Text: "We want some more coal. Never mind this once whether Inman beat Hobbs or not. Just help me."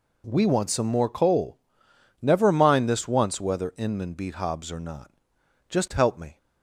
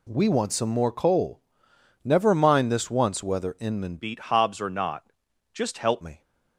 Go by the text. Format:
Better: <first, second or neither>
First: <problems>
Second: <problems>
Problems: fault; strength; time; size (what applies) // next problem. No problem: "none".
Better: first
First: none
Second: changes voice from "beat" to "help"; from 3.9 to 6.0 s; 2.1 s long